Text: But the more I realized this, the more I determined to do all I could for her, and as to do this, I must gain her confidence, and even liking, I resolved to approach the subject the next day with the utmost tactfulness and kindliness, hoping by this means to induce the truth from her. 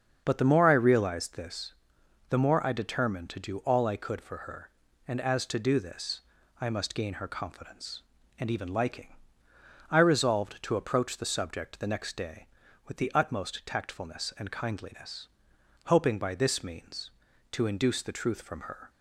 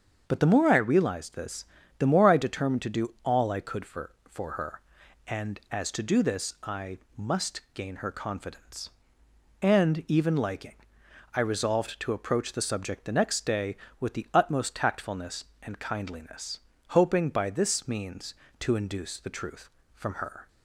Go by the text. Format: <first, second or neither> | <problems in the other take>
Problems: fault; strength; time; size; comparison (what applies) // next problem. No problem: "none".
first | starts louder than the rest; until 1.2 s; 7 dB; also in the first // says "for" twice; at 4.2 s // pauses between "I" and "must"; slight; at 6.9 s; 0.18 s long